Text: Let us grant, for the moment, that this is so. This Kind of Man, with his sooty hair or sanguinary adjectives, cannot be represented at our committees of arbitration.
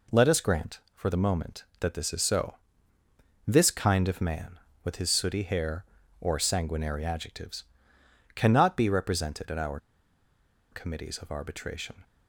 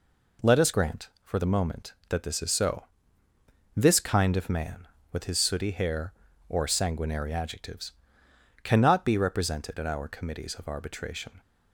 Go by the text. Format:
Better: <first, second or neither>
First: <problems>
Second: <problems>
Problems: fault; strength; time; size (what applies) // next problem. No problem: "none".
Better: second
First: pauses between "our" and "committees"; noticeable; at 9.7 s; 0.94 s long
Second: none